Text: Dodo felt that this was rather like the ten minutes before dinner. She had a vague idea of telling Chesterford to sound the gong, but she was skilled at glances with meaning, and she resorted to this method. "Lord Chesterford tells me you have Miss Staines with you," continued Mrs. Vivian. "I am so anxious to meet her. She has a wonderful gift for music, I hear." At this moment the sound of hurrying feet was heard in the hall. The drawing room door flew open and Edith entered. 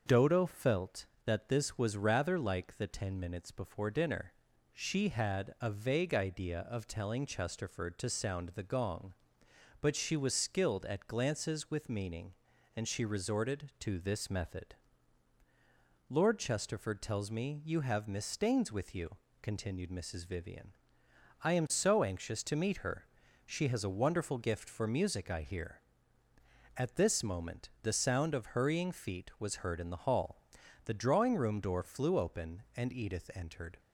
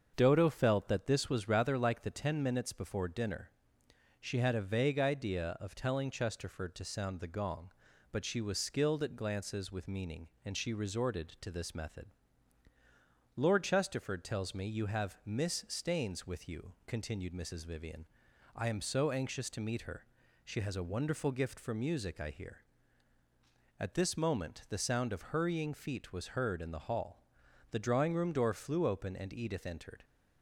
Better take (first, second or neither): neither